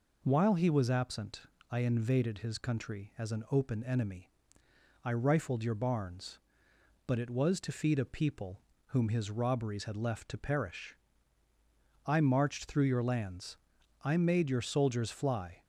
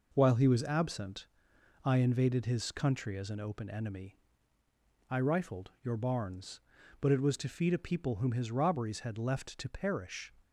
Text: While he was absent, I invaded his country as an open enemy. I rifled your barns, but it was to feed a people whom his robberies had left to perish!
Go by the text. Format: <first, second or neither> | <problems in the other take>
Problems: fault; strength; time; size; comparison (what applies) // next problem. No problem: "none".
second | pauses between "people" and "whom"; slight; at 8.6 s; 0.26 s long // goes on to say "I marched through your lands I made your soldiers fly"; strong; from 12.0 s on; 3.5 s long